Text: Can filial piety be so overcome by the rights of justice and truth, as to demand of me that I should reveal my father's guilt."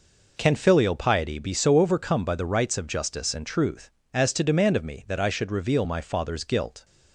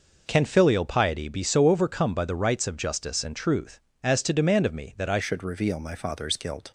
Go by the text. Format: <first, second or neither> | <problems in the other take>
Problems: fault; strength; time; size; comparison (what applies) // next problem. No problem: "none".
first | changes voice at "should"; from 5.2 s on; 1.5 s long